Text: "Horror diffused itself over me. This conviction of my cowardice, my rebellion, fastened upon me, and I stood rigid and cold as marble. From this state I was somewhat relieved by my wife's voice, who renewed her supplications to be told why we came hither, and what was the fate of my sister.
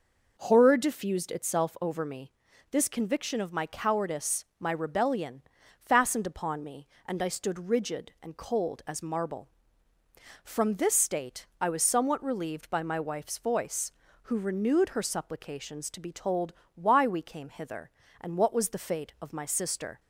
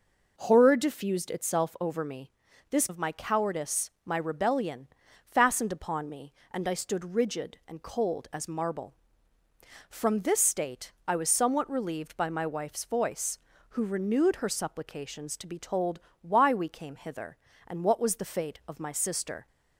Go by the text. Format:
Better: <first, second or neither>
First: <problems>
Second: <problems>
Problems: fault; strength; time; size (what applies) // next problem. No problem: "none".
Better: first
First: pauses between "told" and "why"; slight; at 16.5 s; 0.22 s long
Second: skips "conviction"; at 2.8 s // pauses between "told" and "why"; slight; at 15.9 s; 0.22 s long